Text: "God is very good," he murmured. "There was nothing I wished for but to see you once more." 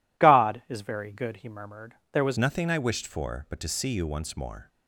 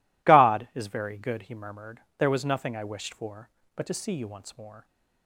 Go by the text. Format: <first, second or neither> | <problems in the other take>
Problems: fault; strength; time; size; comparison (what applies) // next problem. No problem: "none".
second | changes voice at "nothing"; from 2.3 s on; 2.3 s long